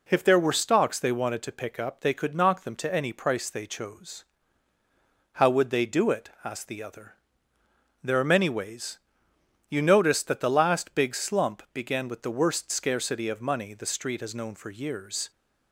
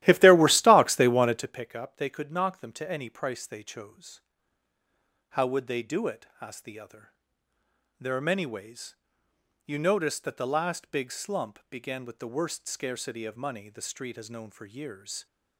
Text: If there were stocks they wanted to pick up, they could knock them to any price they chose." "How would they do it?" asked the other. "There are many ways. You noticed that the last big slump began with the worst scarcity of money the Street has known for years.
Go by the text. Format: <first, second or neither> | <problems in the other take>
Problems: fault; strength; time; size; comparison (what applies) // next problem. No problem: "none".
first | starts louder than the rest; strong; until 1.6 s; 14.5 dB